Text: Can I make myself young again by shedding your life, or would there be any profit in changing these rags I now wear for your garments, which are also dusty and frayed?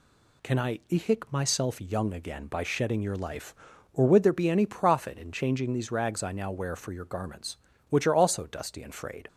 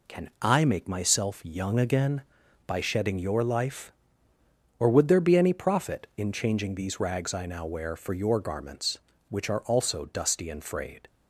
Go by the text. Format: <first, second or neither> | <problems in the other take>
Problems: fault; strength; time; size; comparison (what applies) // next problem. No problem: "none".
second | says "ihik" for "make"; at 0.8 s